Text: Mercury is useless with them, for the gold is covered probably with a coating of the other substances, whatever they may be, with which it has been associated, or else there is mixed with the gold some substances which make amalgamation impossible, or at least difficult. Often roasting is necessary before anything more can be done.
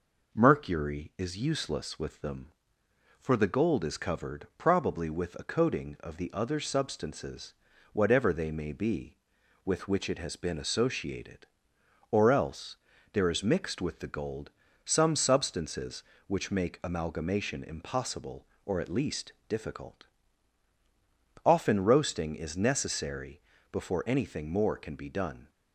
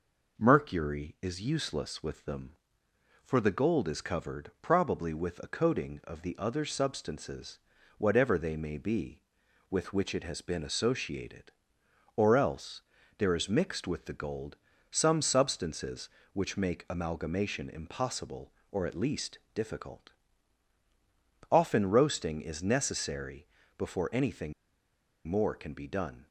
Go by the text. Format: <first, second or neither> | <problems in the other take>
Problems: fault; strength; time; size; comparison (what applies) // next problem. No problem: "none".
first | pauses between "else" and "there"; slight; at 12.8 s; 0.36 s long; slight in the first // pauses between "gold" and "some"; slight; at 14.5 s; 0.34 s long; slight in the first // pauses between "necessary" and "before"; slight; at 23.4 s; 0.32 s long; slight in the first // pauses between "anything" and "more"; noticeable; at 24.5 s; 0.74 s long